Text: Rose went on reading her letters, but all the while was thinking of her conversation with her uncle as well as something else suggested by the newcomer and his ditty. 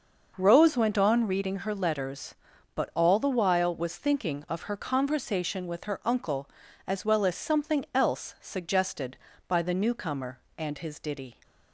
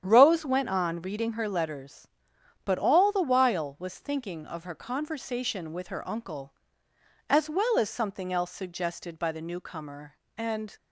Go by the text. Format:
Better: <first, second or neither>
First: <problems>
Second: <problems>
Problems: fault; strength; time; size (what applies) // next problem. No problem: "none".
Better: first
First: starts louder than the rest; noticeable; until 1.3 s; 6 dB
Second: starts louder than the rest; strong; until 1.0 s; 9 dB // stops before "his ditty"; at 10.7 s